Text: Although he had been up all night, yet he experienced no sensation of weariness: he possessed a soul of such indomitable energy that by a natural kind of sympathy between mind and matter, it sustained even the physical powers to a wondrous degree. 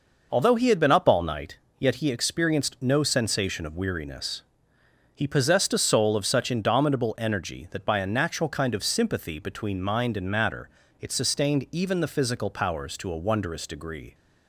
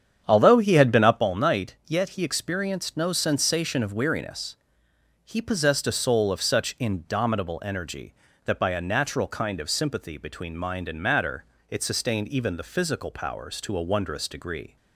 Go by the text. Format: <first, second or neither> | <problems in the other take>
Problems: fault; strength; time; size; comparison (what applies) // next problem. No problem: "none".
first | starts louder than the rest; strong; until 1.3 s; 8.5 dB